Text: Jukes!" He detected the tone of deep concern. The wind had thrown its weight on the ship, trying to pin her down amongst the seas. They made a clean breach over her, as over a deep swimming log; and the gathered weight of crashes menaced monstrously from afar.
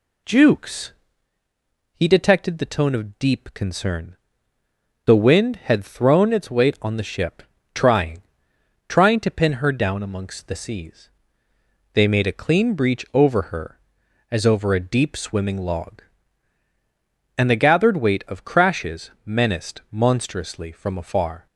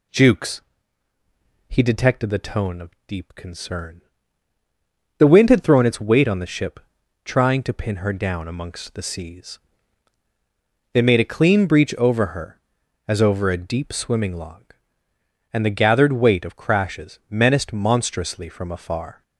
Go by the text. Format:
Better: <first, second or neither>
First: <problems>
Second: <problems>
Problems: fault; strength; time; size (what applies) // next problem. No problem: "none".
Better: second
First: says "trying" twice; at 8.8 s // pauses between "crashes" and "menaced"; slight; at 19.1 s; 0.16 s long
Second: none